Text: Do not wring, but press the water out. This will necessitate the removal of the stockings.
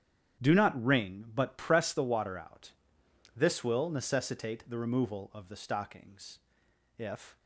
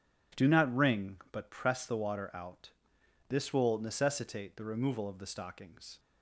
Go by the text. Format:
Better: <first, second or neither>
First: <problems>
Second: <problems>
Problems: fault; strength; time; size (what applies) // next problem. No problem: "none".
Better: second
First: starts louder than the rest; strong; until 1.5 s; 9.5 dB // goes on to say "If"; slight; from 6.9 s on; 0.42 s long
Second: none